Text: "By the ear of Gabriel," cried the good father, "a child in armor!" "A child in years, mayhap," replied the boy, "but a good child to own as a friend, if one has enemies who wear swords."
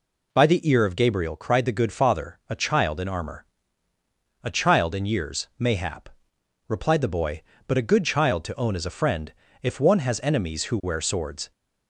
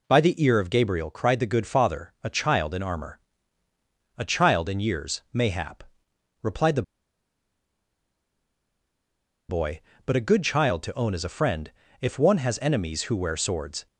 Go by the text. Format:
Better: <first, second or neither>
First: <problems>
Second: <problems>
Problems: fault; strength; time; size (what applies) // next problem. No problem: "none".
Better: first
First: none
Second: pauses between "the" and "boy"; strong; at 6.8 s; 2.6 s long